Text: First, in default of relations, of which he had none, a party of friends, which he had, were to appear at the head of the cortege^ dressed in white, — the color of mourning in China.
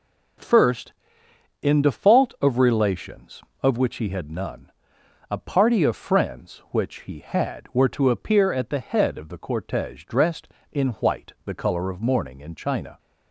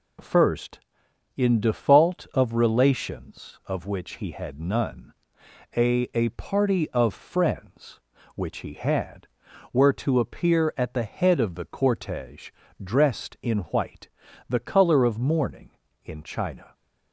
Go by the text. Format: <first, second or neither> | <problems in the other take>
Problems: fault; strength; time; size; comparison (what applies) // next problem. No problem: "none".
first | says "a" twice; at 6.1 s // pauses between "cortege" and "dressed"; slight; at 12.4 s; 0.32 s long